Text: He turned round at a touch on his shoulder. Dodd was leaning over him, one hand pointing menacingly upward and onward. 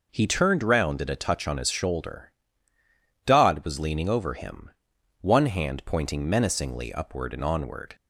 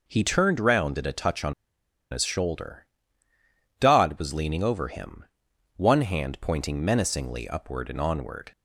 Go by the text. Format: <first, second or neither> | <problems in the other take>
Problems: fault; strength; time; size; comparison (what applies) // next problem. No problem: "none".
first | pauses between "on" and "his"; noticeable; at 1.5 s; 0.58 s long